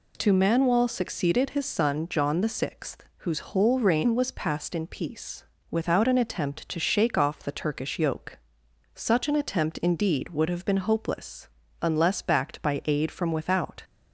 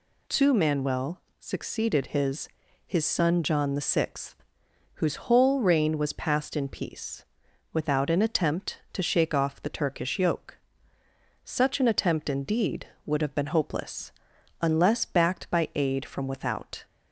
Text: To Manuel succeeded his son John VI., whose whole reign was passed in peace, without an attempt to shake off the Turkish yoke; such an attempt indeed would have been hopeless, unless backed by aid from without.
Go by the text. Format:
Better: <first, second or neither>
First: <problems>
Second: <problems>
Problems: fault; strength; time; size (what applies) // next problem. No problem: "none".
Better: first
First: none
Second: pauses between "Manuel" and "succeeded"; slight; at 1.2 s; 0.18 s long // says "his" twice; at 2.8 s